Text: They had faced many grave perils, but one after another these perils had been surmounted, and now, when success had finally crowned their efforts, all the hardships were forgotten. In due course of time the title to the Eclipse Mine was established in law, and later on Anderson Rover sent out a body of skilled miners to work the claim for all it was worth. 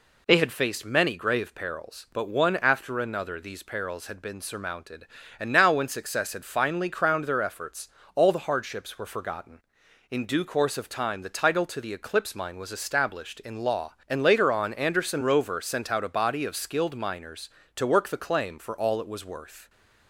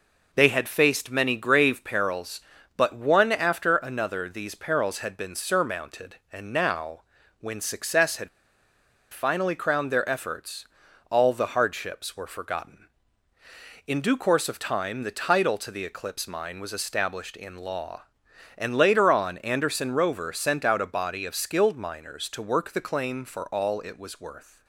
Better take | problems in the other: first | pauses between "had" and "finally"; noticeable; at 8.2 s; 0.85 s long

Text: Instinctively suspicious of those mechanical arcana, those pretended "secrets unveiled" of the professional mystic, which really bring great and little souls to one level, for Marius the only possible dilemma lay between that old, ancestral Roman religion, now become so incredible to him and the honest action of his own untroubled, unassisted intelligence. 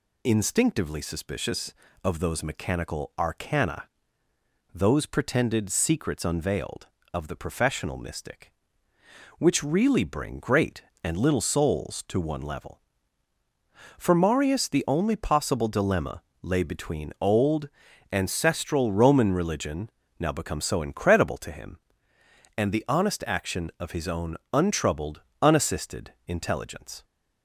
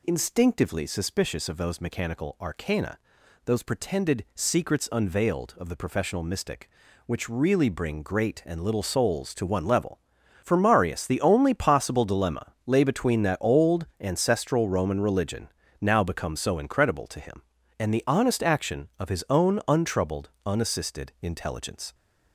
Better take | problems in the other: second | pauses between "dilemma" and "lay"; slight; at 16.2 s; 0.20 s long // skips "that"; at 17.1 s // pauses between "own" and "untroubled"; slight; at 24.3 s; 0.16 s long

